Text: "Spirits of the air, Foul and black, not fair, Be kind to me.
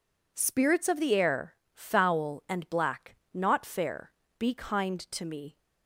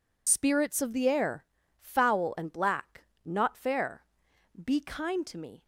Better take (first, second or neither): first